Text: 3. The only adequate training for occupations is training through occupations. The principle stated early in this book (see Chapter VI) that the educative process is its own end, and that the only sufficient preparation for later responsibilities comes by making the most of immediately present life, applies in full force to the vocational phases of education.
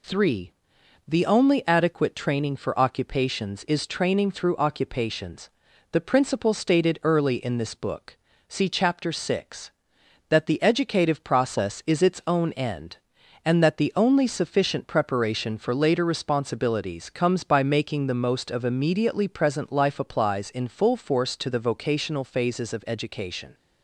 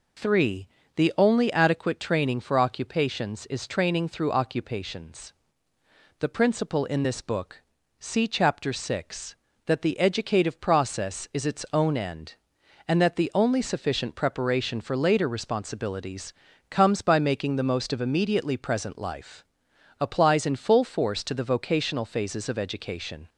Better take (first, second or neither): first